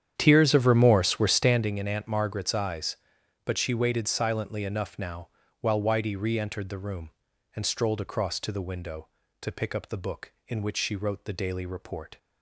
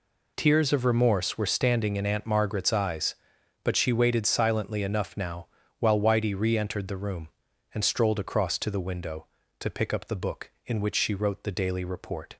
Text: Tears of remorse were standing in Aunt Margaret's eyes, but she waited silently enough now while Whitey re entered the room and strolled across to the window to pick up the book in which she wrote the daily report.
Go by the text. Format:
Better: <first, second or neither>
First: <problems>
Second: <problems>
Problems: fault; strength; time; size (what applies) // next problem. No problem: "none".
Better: second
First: starts louder than the rest; strong; until 1.8 s; 9 dB // pauses between "now" and "while"; slight; at 5.2 s; 0.32 s long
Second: pauses between "now" and "while"; slight; at 5.4 s; 0.32 s long